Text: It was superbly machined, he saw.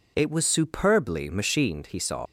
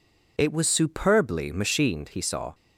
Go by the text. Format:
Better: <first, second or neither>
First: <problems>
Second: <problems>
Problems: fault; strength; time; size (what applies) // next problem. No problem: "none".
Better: second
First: leaves "saw" unfinished; at 2.2 s; 70 ms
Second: none